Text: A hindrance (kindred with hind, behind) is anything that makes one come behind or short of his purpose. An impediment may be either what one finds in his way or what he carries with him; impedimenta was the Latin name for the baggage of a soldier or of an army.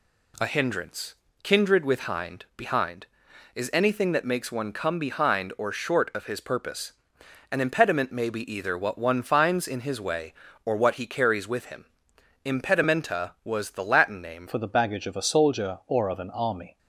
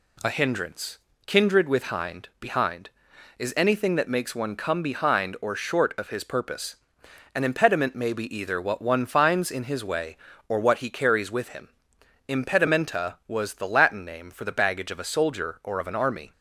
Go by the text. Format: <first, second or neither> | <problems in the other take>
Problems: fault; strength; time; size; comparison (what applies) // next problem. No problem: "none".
second | changes voice at "for"; from 14.4 s on; 2.3 s long